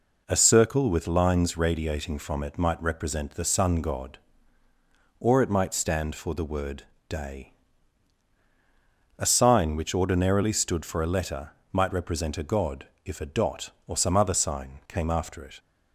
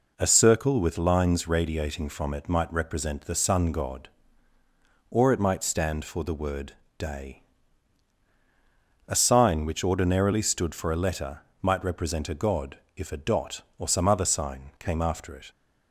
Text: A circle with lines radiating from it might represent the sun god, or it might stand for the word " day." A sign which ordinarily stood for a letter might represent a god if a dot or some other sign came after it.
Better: neither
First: pauses between "letter" and "might"; slight; at 11.5 s; 0.22 s long // pauses between "god" and "if"; slight; at 12.8 s; 0.18 s long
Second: pauses between "letter" and "might"; slight; at 11.3 s; 0.22 s long // pauses between "god" and "if"; slight; at 12.7 s; 0.18 s long

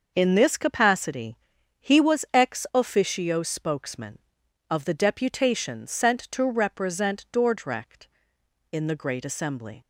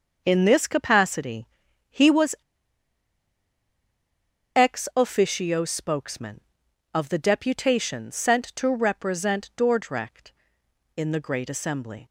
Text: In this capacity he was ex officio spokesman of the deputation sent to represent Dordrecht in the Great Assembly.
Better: first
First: pauses between "capacity" and "he"; at 1.3 s; 0.42 s long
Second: pauses between "capacity" and "he"; at 1.4 s; 0.42 s long // pauses between "was" and "ex"; strong; at 2.3 s; 2.2 s long

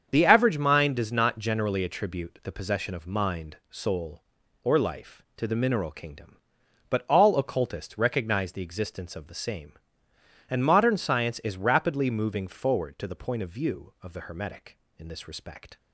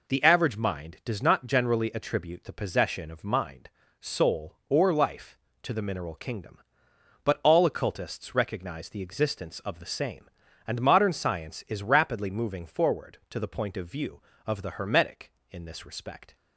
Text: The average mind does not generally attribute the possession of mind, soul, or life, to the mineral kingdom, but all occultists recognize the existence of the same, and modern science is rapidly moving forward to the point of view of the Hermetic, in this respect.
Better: second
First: loses the start of "The"; at 0.0 s; 30 ms // starts louder than the rest; strong; until 1.1 s; 7.5 dB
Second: none

